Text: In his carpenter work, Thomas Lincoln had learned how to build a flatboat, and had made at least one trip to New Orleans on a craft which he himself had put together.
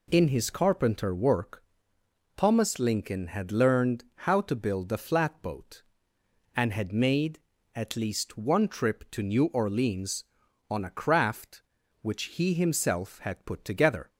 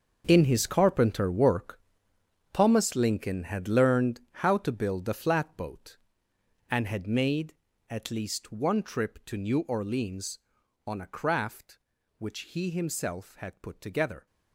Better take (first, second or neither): first